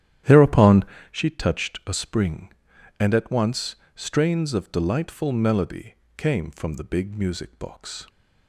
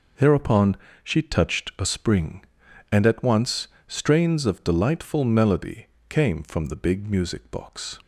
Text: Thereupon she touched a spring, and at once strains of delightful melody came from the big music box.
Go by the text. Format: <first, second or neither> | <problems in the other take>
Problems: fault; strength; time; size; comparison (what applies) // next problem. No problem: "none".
second | starts louder than the rest; strong; until 1.2 s; 11.5 dB // pauses between "Thereupon" and "she"; slight; at 0.8 s; 0.28 s long; slight in the second // pauses between "once" and "strains"; slight; at 3.7 s; 0.20 s long; slight in the second // pauses between "melody" and "came"; slight; at 5.9 s; 0.20 s long; slight in the second